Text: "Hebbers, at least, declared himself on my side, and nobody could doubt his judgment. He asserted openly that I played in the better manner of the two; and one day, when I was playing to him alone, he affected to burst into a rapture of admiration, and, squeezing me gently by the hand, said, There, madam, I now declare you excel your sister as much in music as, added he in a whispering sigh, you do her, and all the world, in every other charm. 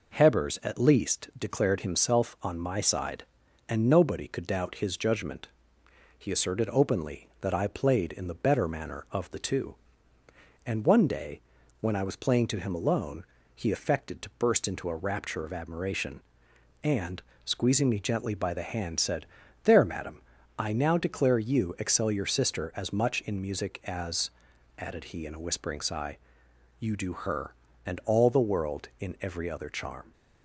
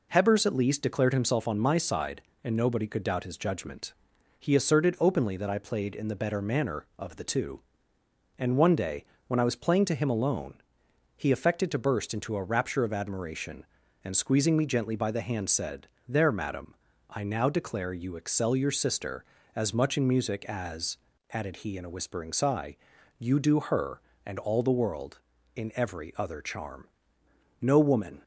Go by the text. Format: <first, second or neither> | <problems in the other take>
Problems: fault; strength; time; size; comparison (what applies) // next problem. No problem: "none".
first | goes on to say "No woman"; noticeable; from 27.6 s on; 0.62 s long